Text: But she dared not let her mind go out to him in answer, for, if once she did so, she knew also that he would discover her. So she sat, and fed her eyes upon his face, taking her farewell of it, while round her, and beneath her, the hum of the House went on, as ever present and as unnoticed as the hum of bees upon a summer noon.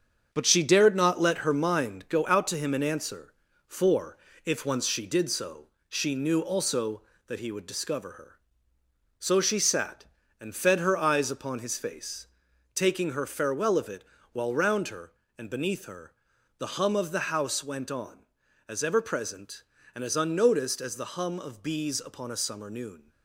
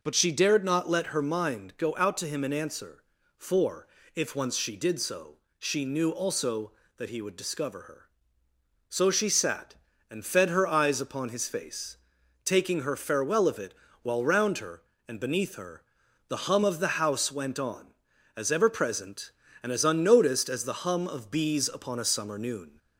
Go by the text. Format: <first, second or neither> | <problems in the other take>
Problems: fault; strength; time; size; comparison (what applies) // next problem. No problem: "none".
second | gets quieter; throughout; 6.5 dB